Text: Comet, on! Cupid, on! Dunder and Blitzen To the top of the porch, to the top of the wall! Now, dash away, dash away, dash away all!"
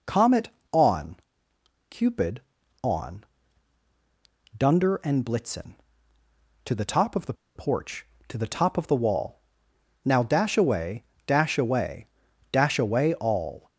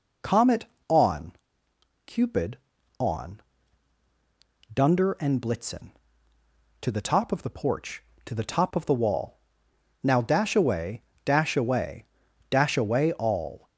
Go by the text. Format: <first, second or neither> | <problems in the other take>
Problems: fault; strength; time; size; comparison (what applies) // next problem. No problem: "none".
second | pauses between "the" and "porch"; slight; at 7.3 s; 0.22 s long